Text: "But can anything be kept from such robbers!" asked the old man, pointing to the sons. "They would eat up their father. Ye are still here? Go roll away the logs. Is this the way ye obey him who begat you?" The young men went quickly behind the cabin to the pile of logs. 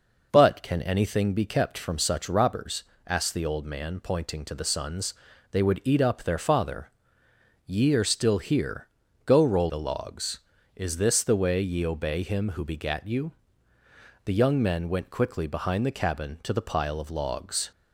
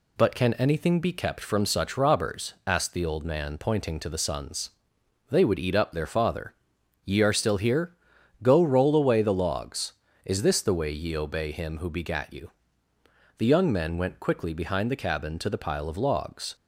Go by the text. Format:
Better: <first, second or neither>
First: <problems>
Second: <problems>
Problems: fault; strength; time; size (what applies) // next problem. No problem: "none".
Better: second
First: skips "away"; at 9.6 s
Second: none